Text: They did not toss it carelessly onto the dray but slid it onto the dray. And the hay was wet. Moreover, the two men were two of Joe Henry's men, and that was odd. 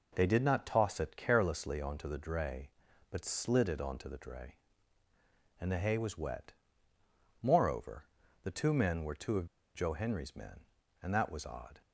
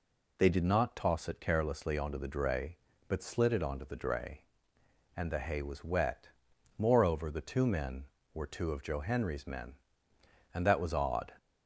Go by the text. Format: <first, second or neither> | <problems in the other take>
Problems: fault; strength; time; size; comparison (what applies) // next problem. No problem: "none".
second | pauses between "of" and "Joe"; slight; at 9.4 s; 0.29 s long